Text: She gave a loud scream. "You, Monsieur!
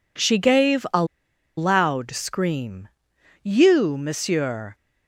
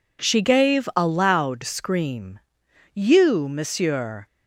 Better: second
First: pauses between "a" and "loud"; noticeable; at 1.0 s; 0.52 s long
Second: none

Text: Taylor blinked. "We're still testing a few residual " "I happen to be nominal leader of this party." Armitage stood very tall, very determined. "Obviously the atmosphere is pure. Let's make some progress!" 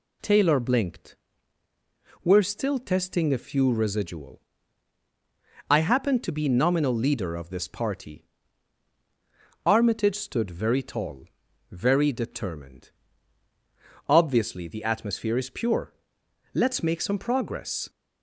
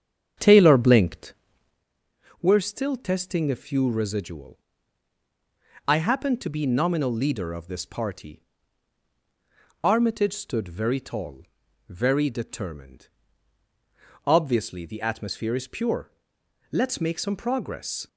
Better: first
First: none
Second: starts louder than the rest; strong; until 1.8 s; 8.5 dB

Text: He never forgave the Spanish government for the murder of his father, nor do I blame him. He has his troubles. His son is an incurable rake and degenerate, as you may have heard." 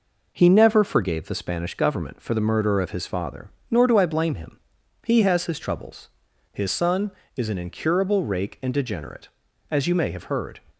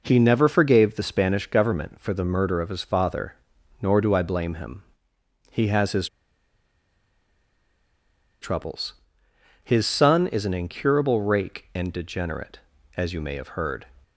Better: first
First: none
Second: pauses between "his" and "troubles"; strong; at 6.0 s; 2.3 s long

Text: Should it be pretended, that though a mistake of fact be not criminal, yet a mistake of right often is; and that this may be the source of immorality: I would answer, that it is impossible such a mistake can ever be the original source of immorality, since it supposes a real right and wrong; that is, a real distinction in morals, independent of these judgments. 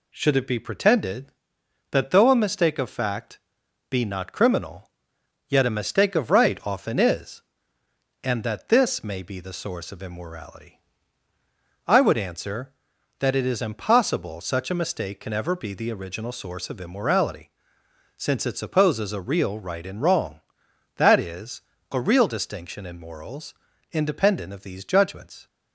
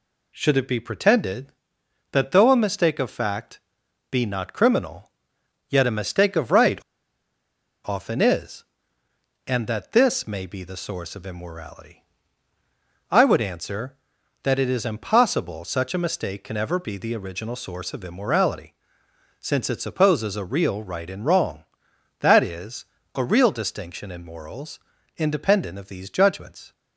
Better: first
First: pauses between "fact" and "be"; noticeable; at 3.3 s; 0.50 s long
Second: pauses between "fact" and "be"; noticeable; at 3.5 s; 0.50 s long // pauses between "right" and "often"; at 6.7 s; 1.0 s long

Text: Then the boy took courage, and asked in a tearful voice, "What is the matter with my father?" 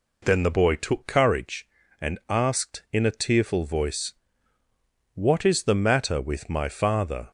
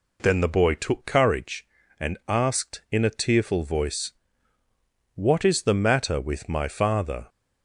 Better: neither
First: none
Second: none

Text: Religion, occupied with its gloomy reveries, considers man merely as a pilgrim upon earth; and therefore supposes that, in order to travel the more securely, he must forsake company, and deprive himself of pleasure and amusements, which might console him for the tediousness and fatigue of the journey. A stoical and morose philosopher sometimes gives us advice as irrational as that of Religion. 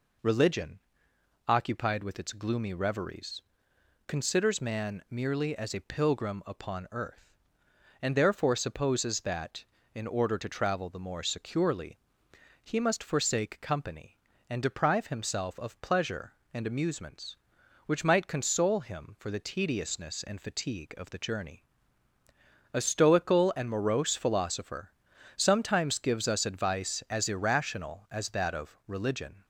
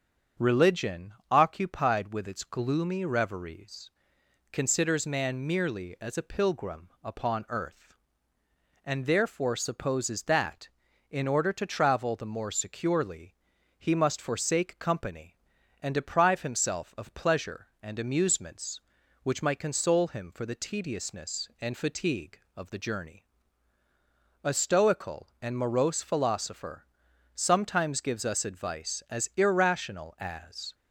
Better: first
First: pauses between "philosopher" and "sometimes"; noticeable; at 24.9 s; 0.46 s long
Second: starts louder than the rest; strong; until 1.5 s; 7.5 dB // pauses between "philosopher" and "sometimes"; noticeable; at 26.8 s; 0.50 s long // stops before "that of Religion"; at 30.7 s

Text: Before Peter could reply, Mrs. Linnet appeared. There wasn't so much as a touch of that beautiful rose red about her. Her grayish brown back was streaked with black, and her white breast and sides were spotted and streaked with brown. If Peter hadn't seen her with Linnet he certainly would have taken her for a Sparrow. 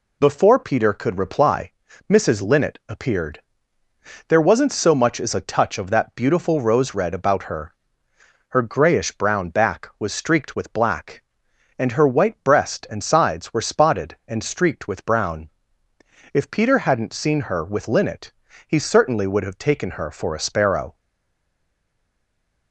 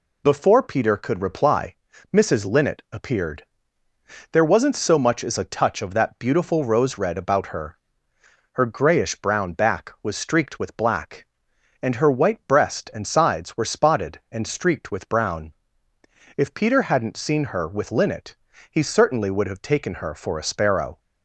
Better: second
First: pauses between "Linnet" and "he"; at 18.3 s; 0.38 s long // stays silent after the last word; noticeable; from 20.9 s on; 1.8 s long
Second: pauses between "Linnet" and "he"; at 18.3 s; 0.38 s long

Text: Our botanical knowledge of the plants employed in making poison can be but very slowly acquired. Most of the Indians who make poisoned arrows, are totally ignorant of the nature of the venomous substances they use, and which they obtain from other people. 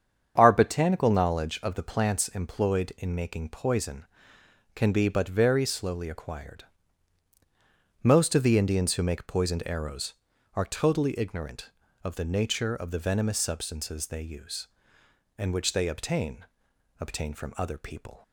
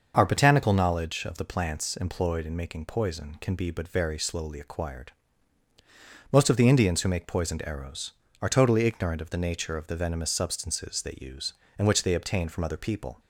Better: second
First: starts louder than the rest; strong; until 1.3 s; 8 dB // says "obtain" twice; at 16.9 s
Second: starts louder than the rest; until 1.1 s; 6 dB

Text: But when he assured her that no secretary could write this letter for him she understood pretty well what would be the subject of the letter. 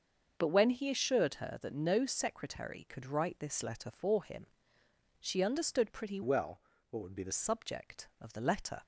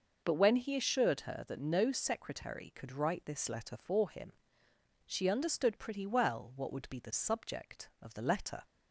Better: second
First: starts louder than the rest; until 1.3 s; 6.5 dB // pauses between "him" and "she"; noticeable; at 4.4 s; 0.74 s long // changes voice from "well" to "the"; from 6.2 to 7.3 s; 1.1 s long // pauses between "well" and "what"; slight; at 6.6 s; 0.28 s long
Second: pauses between "him" and "she"; noticeable; at 4.3 s; 0.74 s long

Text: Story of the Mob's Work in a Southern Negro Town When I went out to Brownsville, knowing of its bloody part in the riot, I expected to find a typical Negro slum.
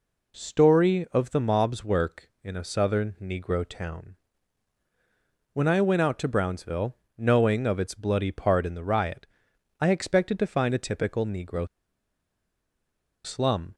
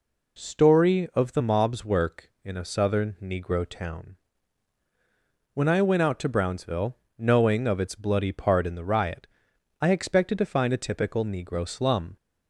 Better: second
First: pauses between "Town" and "When"; strong; at 4.1 s; 1.3 s long // pauses between "Negro" and "slum"; strong; at 11.6 s; 1.5 s long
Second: pauses between "Town" and "When"; strong; at 4.1 s; 1.3 s long

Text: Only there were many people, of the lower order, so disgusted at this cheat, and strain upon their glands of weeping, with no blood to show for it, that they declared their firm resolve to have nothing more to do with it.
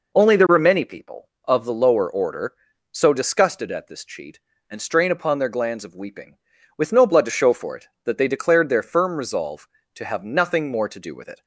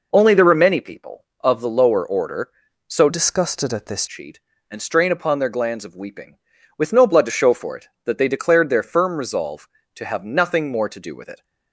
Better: first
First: none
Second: changes voice from "disgusted" to "this"; from 3.0 to 4.0 s; 1.0 s long

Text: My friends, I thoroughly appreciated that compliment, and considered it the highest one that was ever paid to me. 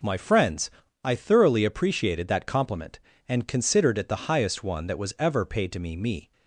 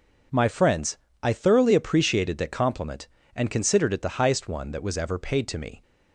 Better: second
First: says "me" twice; at 5.9 s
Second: none

